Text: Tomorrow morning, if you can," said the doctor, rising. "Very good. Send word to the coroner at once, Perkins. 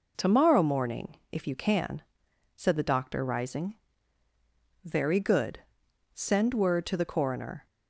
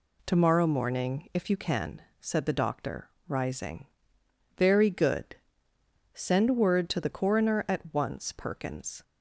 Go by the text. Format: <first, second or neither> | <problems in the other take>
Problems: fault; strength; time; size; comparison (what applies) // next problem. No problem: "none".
second | stops before "at once Perkins"; at 7.6 s